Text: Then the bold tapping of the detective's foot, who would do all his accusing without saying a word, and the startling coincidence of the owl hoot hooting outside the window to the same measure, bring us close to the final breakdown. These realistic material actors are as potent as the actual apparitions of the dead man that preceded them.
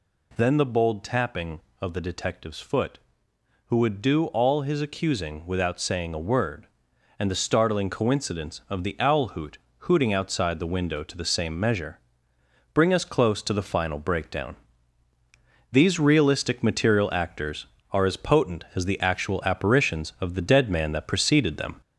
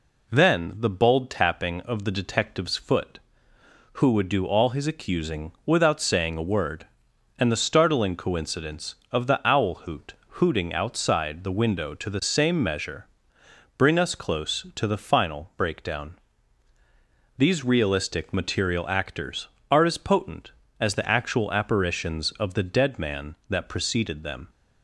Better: second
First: gets louder; throughout; 3.5 dB // pauses between "hoot" and "hooting"; slight; at 9.5 s; 0.22 s long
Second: pauses between "hoot" and "hooting"; slight; at 10.1 s; 0.18 s long

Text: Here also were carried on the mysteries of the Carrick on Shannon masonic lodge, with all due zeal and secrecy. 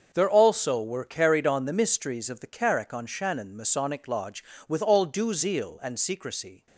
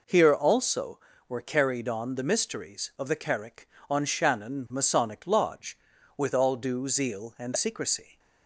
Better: second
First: starts louder than the rest; until 1.1 s; 6.5 dB // says "There" for "Here"; at 0.1 s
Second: none

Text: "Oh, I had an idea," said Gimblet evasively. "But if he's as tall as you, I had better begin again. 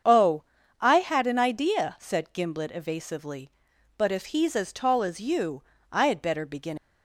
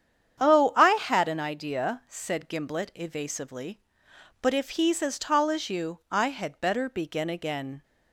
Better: second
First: starts louder than the rest; strong; until 1.4 s; 7 dB // stops before "again"; at 6.7 s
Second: starts louder than the rest; strong; until 1.4 s; 8.5 dB

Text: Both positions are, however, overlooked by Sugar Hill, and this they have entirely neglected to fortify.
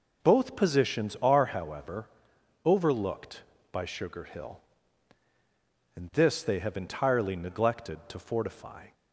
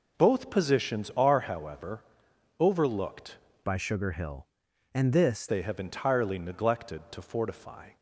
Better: first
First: none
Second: changes voice from "by" to "this"; from 3.6 to 5.4 s; 1.8 s long

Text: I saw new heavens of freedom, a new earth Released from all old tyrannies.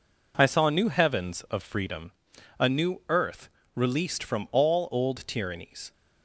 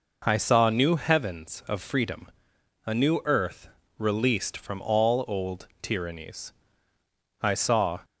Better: first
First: pauses between "earth" and "Released"; slight; at 3.4 s; 0.26 s long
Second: pauses between "earth" and "Released"; slight; at 3.6 s; 0.32 s long // goes on to say "I saw"; from 7.4 s on; 0.58 s long

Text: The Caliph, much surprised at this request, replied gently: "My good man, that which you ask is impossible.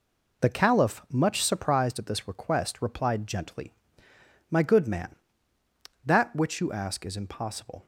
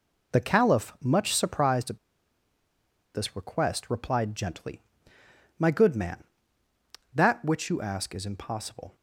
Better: first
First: none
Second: pauses between "at" and "this"; at 1.9 s; 1.1 s long

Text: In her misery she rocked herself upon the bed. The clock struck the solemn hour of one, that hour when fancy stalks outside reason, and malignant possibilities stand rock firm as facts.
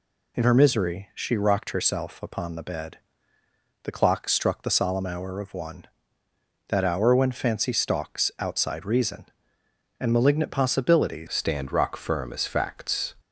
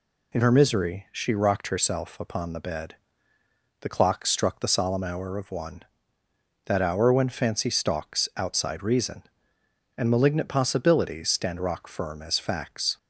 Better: second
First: changes voice at "stand"; from 11.2 s on; 1.9 s long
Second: none

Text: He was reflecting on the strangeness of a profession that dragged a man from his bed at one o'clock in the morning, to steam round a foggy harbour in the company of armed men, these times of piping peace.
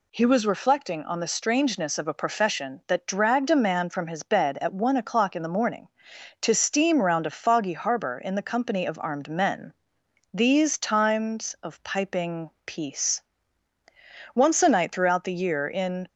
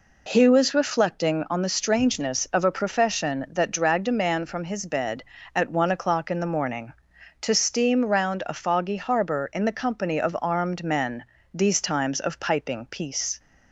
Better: second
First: pauses between "piping" and "peace"; slight; at 12.4 s; 0.16 s long // goes on to say "Once a night throughout the year in"; strong; from 14.3 s on; 1.7 s long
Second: none

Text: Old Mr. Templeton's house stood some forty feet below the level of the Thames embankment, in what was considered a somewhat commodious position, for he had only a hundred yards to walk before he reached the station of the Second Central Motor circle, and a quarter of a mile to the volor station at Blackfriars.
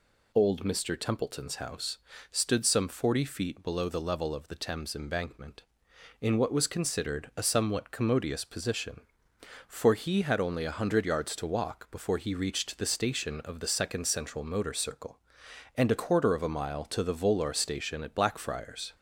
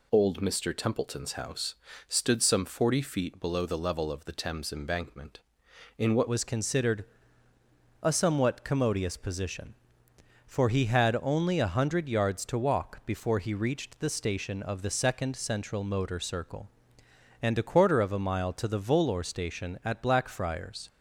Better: first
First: pauses between "house" and "stood"; slight; at 1.9 s; 0.34 s long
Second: pauses between "house" and "stood"; slight; at 1.7 s; 0.34 s long // changes voice at "was"; from 6.2 s on; 14.6 s long // pauses between "considered" and "a"; noticeable; at 7.0 s; 0.98 s long

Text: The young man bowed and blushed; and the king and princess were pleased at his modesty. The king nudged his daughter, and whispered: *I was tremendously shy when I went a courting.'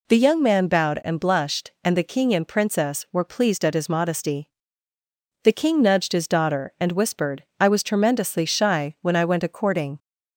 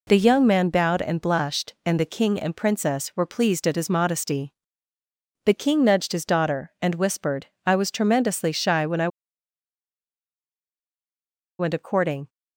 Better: first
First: none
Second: pauses between "I" and "went"; strong; at 9.0 s; 2.5 s long

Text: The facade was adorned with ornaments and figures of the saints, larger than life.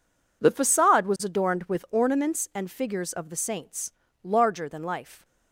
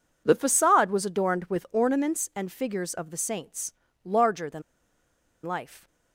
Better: first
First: none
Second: pauses between "than" and "life"; noticeable; at 4.6 s; 0.82 s long

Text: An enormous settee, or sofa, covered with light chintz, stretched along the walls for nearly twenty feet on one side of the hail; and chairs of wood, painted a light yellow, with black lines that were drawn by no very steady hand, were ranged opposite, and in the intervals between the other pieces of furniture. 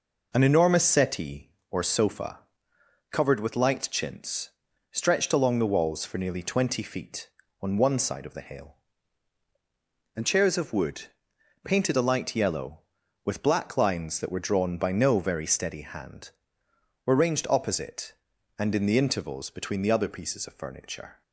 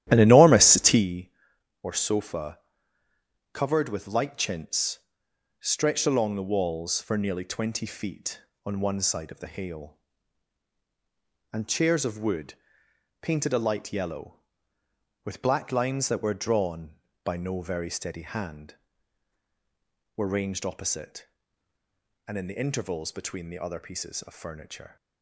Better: first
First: none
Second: starts louder than the rest; strong; until 1.0 s; 12.5 dB

